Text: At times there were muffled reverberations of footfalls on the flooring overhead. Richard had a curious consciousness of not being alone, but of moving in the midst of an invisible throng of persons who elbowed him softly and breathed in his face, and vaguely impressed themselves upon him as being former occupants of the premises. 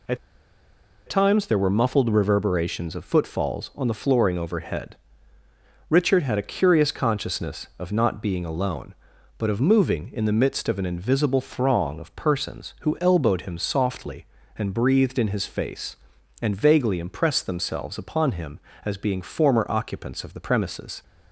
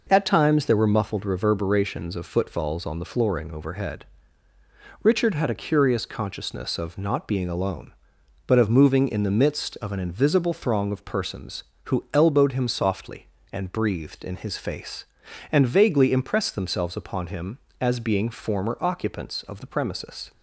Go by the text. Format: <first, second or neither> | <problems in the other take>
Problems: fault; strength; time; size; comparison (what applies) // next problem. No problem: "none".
second | pauses between "At" and "times"; noticeable; at 0.1 s; 0.90 s long